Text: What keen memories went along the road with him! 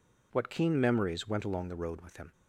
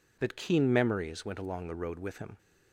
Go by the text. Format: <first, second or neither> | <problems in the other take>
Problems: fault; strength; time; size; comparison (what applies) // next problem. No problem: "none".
first | says "That" for "What"; at 0.1 s